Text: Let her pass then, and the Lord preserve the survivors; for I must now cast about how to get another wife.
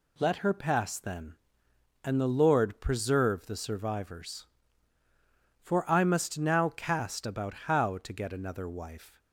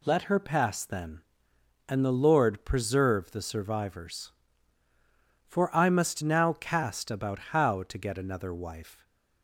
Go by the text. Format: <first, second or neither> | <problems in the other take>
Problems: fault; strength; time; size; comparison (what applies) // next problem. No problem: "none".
neither | none